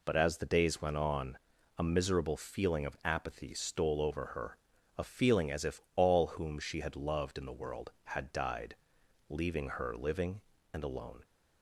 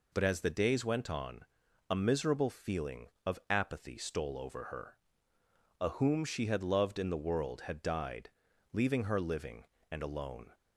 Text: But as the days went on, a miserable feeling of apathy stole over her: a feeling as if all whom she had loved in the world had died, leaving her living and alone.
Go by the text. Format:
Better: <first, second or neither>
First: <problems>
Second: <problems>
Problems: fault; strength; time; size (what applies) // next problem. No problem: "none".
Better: first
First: none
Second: skips "feeling as if all"; at 5.8 s